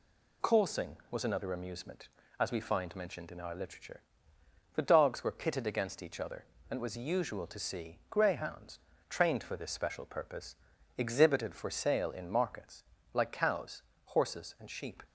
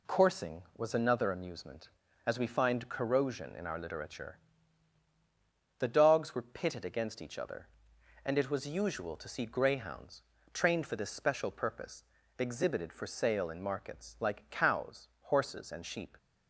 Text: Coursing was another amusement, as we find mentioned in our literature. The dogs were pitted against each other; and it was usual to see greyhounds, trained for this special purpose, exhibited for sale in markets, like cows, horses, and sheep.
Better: first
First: none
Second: says "corrosion" for "mentioned"; at 2.8 s

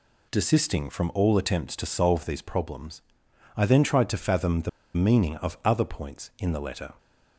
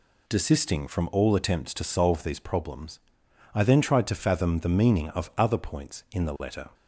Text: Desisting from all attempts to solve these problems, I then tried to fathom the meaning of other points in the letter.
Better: second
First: pauses between "the" and "meaning"; slight; at 4.6 s; 0.25 s long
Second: none

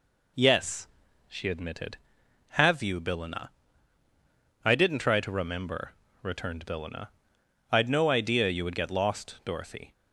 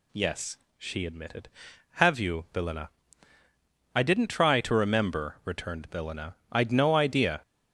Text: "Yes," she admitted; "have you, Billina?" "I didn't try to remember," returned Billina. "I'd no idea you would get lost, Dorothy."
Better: first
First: none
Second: stops before "you would get lost Dorothy"; at 7.4 s

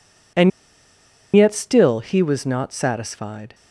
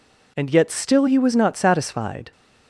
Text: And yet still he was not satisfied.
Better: second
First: pauses between "And" and "yet"; noticeable; at 0.5 s; 0.86 s long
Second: none

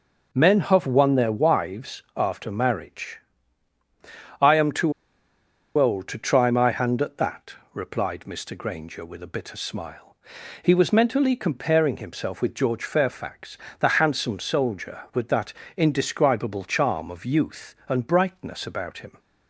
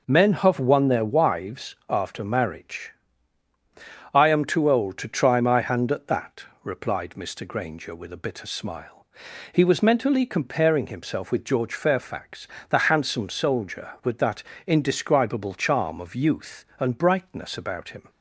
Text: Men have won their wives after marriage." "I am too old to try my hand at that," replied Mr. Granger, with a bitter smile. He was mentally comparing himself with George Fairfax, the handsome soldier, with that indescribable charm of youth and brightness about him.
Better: second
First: pauses between "too" and "old"; noticeable; at 4.9 s; 0.85 s long // pauses between "that" and "indescribable"; slight; at 15.5 s; 0.24 s long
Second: pauses between "that" and "indescribable"; slight; at 14.4 s; 0.24 s long

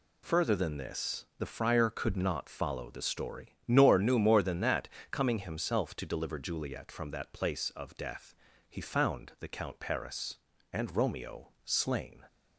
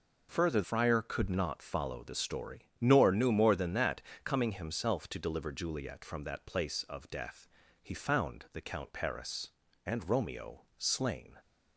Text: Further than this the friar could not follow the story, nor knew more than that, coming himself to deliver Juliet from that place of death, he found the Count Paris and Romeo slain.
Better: first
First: pauses between "Romeo" and "slain"; slight; at 11.4 s; 0.16 s long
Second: skips "than this the"; at 0.6 s // pauses between "Romeo" and "slain"; slight; at 10.6 s; 0.16 s long

